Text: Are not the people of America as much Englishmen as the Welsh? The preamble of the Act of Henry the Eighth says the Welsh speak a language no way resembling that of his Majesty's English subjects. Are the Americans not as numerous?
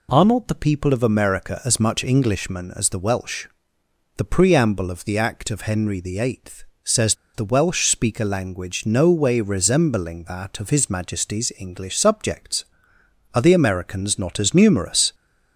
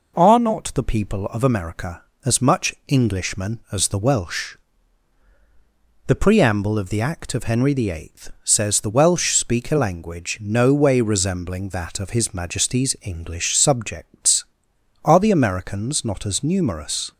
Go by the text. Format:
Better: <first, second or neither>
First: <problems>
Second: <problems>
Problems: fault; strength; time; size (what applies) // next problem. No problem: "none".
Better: second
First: pauses between "Eighth" and "says"; slight; at 6.6 s; 0.18 s long // pauses between "says" and "the"; slight; at 7.1 s; 0.20 s long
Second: none